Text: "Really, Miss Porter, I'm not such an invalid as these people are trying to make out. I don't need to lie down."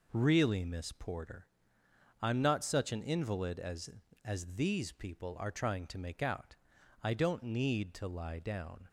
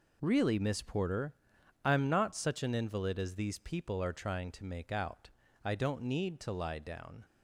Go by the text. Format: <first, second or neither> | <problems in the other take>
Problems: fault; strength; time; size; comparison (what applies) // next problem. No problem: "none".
second | says "as" twice; at 4.2 s